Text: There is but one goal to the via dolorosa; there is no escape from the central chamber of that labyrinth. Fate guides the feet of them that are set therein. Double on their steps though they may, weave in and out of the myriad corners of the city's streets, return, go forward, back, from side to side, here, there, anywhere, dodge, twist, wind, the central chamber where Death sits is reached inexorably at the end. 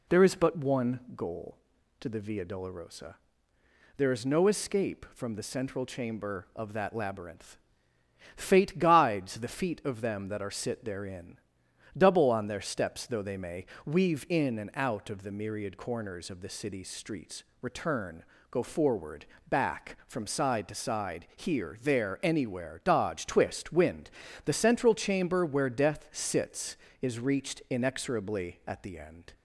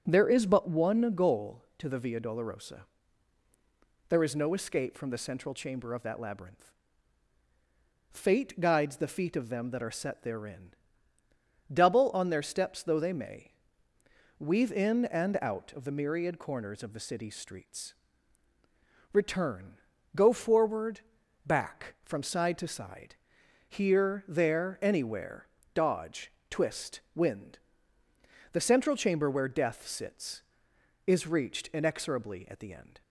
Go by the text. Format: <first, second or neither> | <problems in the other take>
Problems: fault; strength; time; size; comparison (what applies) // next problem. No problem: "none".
second | says "sit" for "set"; at 10.5 s